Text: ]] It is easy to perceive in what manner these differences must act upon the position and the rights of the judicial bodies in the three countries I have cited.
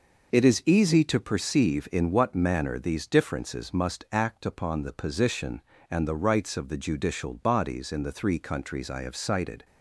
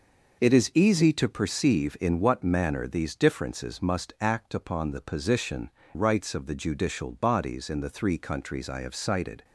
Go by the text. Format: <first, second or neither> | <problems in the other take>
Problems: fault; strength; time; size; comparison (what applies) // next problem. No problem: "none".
first | skips "and the"; at 5.8 s